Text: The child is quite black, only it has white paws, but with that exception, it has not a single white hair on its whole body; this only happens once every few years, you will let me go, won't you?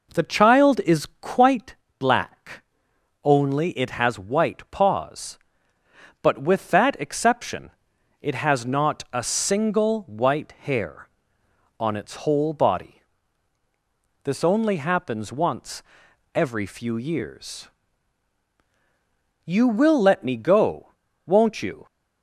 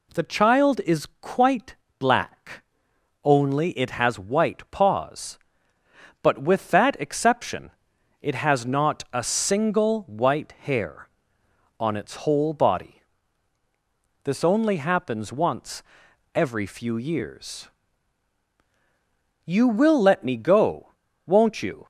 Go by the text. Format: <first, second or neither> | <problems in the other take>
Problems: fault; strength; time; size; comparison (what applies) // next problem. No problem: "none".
second | starts louder than the rest; noticeable; until 1.7 s; 4.5 dB // pauses between "is" and "quite"; slight; at 1.0 s; 0.16 s long; slight in the second // pauses between "quite" and "black"; slight; at 1.7 s; 0.24 s long; slight in the second // pauses between "once" and "every"; noticeable; at 15.8 s; 0.50 s long; noticeable in the second